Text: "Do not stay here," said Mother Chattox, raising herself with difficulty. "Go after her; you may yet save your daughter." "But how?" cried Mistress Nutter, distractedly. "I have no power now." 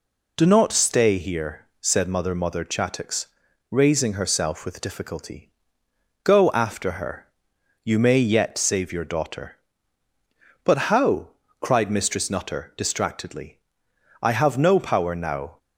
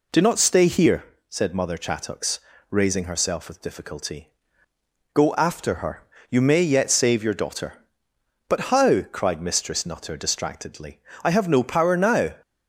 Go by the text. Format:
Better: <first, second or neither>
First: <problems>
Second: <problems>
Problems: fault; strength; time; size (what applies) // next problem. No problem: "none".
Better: second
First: says "Mother" twice; at 2.3 s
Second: none